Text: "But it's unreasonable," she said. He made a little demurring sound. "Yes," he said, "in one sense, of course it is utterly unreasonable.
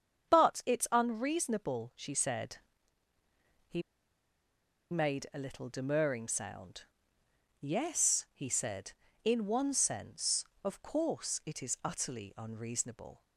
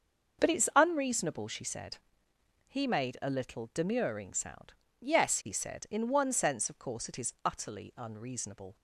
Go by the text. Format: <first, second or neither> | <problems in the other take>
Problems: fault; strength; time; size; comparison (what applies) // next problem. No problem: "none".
second | starts louder than the rest; strong; until 1.3 s; 7.5 dB; also in the second // pauses between "He" and "made"; at 3.8 s; 1.1 s long